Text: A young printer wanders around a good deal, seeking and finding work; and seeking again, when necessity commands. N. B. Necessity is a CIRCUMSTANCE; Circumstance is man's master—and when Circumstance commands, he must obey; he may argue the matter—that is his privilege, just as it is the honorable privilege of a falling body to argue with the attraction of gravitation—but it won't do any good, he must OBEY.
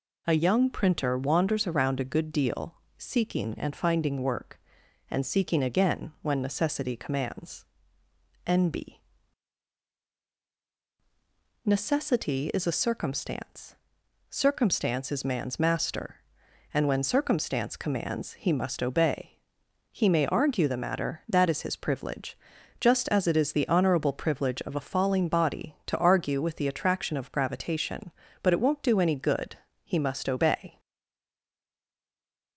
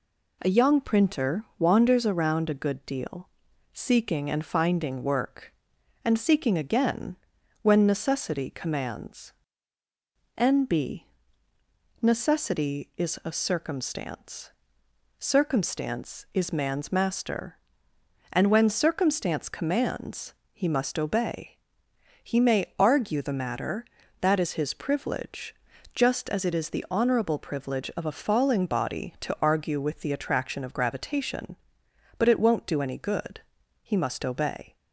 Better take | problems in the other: second | pauses between "B" and "Necessity"; strong; at 8.9 s; 2.6 s long; noticeable in the second // stays silent after the last word; noticeable; from 30.7 s on; 1.8 s long

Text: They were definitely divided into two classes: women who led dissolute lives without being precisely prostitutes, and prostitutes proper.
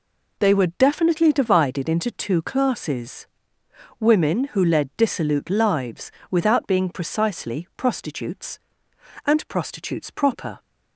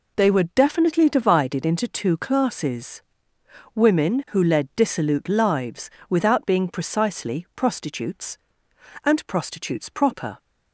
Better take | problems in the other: neither | pauses between "lives" and "without"; slight; the same in both

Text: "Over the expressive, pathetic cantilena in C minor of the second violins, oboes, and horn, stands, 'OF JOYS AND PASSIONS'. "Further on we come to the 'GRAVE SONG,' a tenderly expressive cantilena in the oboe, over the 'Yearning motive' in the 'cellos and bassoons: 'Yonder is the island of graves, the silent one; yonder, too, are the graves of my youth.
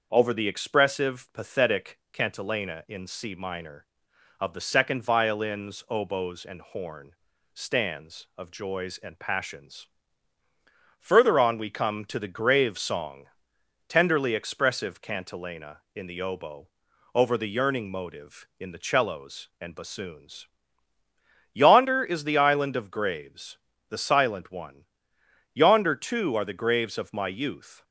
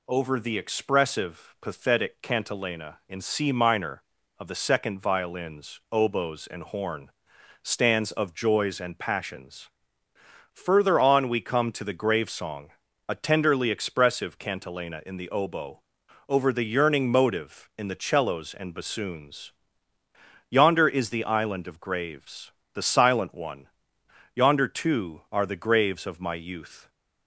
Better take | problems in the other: second | starts louder than the rest; noticeable; until 1.1 s; 6 dB // skips "a"; at 13.5 s

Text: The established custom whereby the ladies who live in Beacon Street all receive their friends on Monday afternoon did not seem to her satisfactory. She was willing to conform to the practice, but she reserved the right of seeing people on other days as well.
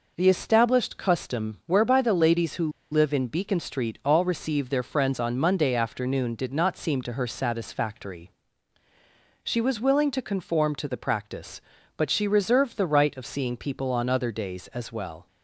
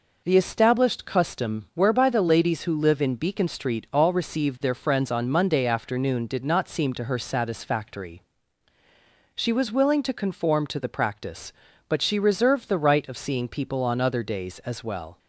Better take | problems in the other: second | pauses between "who" and "live"; slight; at 2.6 s; 0.22 s long

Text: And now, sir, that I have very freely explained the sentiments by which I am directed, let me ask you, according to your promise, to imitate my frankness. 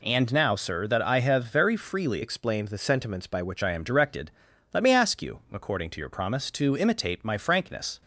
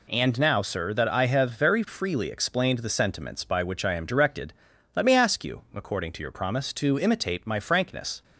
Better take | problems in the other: second | changes voice from "explained" to "which"; from 2.2 to 3.6 s; 1.4 s long

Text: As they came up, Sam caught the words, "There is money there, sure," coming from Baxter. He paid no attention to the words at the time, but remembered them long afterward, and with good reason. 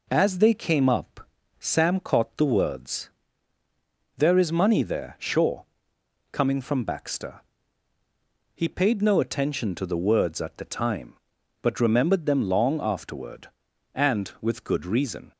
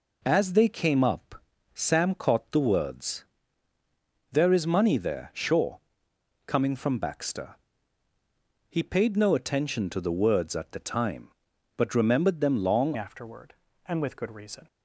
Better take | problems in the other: first | changes voice at "afterward"; from 12.9 s on; 1.7 s long

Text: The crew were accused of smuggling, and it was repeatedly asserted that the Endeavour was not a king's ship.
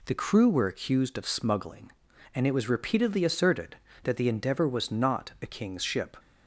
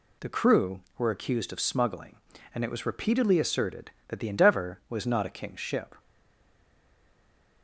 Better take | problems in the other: first | stays silent after the last word; noticeable; from 5.9 s on; 1.7 s long

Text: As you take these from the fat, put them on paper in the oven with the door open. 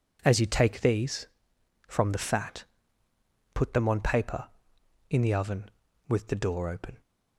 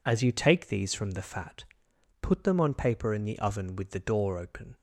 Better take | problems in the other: neither | none

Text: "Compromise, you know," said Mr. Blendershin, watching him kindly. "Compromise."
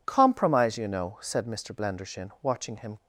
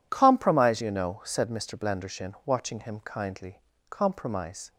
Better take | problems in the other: second | stops before "kindly Compromise"; at 2.9 s

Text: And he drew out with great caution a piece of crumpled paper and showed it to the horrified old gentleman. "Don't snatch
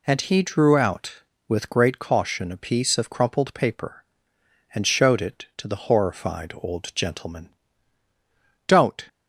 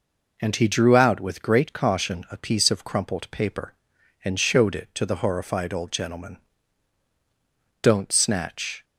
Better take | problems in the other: second | stops before "snatch"; at 9.0 s

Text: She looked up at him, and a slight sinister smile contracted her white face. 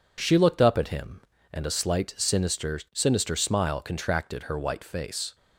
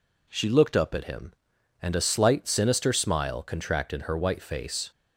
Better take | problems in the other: second | says "sinister" twice; at 2.9 s

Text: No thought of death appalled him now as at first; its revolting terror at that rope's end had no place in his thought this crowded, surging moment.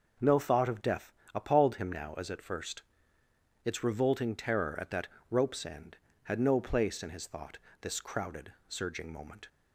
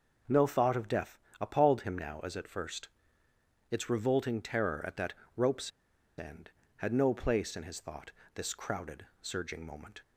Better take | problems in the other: first | pauses between "death" and "appalled"; slight; at 1.1 s; 0.20 s long; slight in the first // pauses between "that" and "rope's"; slight; at 5.1 s; 0.24 s long; slight in the first // pauses between "rope's" and "end"; noticeable; at 5.7 s; 0.47 s long // pauses between "thought" and "this"; slight; at 8.1 s; 0.24 s long; slight in the first

